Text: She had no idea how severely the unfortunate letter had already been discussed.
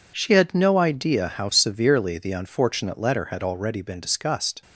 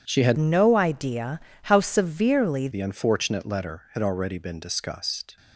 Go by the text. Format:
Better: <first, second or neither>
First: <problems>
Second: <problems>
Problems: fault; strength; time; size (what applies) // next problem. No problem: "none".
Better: first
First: none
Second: changes voice from "no" to "severely"; from 0.3 to 2.6 s; 2.3 s long // pauses between "idea" and "how"; slight; at 1.4 s; 0.22 s long